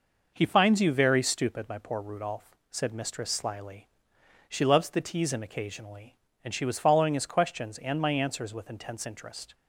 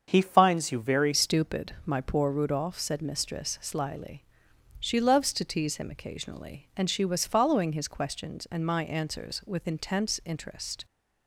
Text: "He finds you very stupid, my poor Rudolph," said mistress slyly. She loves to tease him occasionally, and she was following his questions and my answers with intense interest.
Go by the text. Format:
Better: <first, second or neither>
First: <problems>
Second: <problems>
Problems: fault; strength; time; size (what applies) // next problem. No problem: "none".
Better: first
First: none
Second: starts louder than the rest; until 1.0 s; 7 dB // changes voice at "stupid"; from 1.1 s on; 9.7 s long